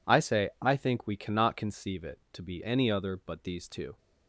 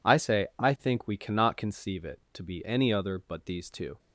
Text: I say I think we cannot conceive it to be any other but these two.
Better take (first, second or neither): neither